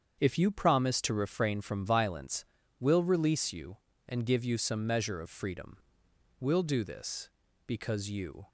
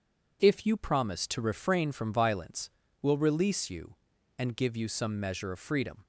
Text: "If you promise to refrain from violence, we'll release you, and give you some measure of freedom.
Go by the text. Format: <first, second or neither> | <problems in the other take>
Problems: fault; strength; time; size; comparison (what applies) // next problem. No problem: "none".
second | starts louder than the rest; strong; until 1.2 s; 7.5 dB // goes on to say "We'll do this because you"; strong; from 6.4 s on; 2.0 s long